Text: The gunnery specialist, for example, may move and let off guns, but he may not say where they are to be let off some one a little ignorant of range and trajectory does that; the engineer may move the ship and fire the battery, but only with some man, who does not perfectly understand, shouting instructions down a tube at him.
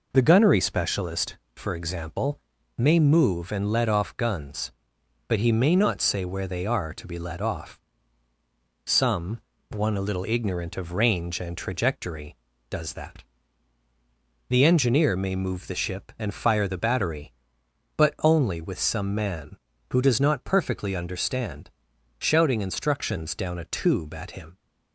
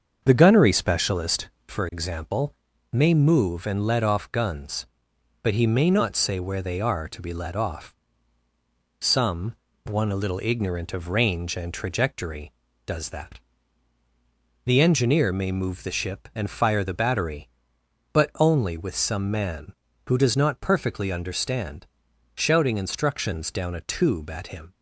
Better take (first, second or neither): first